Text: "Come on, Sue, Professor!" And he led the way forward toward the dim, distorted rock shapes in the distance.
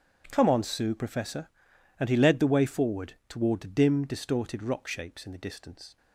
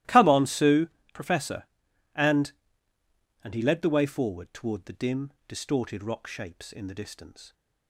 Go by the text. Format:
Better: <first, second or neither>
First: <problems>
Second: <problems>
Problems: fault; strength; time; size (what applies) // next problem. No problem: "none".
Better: first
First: starts louder than the rest; strong; until 1.3 s; 8.5 dB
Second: starts louder than the rest; strong; until 1.3 s; 15.5 dB // says "And" twice; at 3.4 s